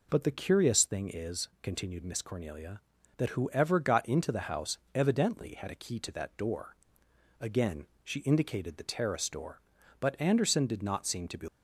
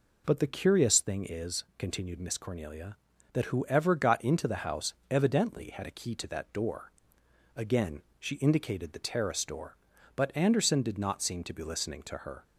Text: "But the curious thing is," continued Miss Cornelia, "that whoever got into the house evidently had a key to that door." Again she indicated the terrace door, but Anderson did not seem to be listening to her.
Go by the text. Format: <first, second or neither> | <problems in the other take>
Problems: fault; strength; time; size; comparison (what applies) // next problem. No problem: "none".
second | pauses between "Again" and "she"; slight; at 7.8 s; 0.18 s long; slight in the second // stops before "listening to her"; at 11.4 s